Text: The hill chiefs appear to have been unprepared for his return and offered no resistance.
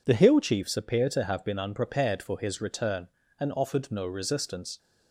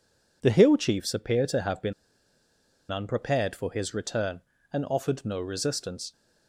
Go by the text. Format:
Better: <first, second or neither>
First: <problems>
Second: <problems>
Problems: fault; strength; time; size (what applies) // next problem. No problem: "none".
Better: first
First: none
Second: pauses between "been" and "unprepared"; at 1.9 s; 0.98 s long